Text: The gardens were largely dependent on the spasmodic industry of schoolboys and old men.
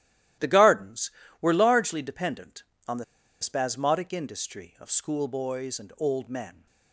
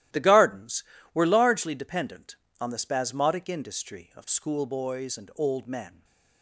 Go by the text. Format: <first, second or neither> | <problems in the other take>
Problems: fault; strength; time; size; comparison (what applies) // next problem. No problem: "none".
second | starts louder than the rest; strong; until 1.6 s; 14 dB; strong in the second // pauses between "the" and "spasmodic"; at 3.0 s; 0.37 s long